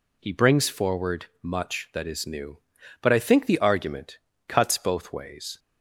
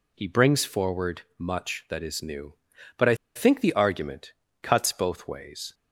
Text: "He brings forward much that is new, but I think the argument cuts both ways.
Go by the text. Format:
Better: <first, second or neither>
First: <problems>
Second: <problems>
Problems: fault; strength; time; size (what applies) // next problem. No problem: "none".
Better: first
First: pauses between "forward" and "much"; slight; at 1.2 s; 0.16 s long // pauses between "argument" and "cuts"; slight; at 4.1 s; 0.30 s long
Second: pauses between "forward" and "much"; slight; at 1.2 s; 0.16 s long // pauses between "I" and "think"; slight; at 3.1 s; 0.20 s long // pauses between "argument" and "cuts"; slight; at 4.3 s; 0.30 s long